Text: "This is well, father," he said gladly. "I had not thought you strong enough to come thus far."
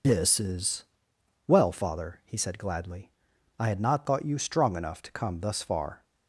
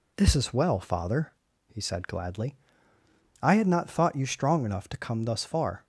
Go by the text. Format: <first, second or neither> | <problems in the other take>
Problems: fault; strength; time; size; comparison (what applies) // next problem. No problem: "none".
second | loses the start of "This"; at 0.0 s; 35 ms // pauses between "is" and "well"; noticeable; at 0.8 s; 0.64 s long